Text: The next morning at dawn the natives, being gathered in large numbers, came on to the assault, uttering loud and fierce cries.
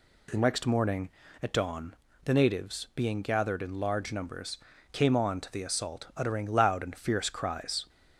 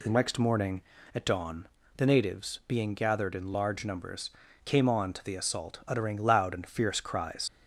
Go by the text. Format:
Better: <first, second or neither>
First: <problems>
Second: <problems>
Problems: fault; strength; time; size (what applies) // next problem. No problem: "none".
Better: first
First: pauses between "dawn" and "the"; slight; at 1.9 s; 0.30 s long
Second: pauses between "dawn" and "the"; slight; at 1.6 s; 0.30 s long // leaves "cries" unfinished; at 7.4 s; 115 ms